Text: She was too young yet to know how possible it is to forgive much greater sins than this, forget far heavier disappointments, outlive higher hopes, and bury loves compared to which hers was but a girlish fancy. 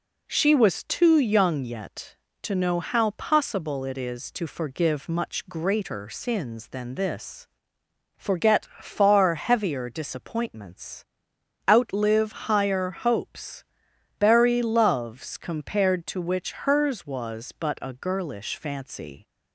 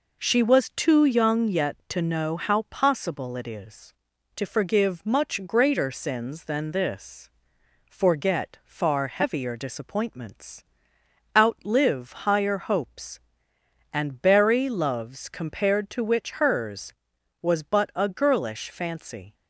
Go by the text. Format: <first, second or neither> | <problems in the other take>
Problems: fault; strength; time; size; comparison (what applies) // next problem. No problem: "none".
second | skips "and"; at 13.9 s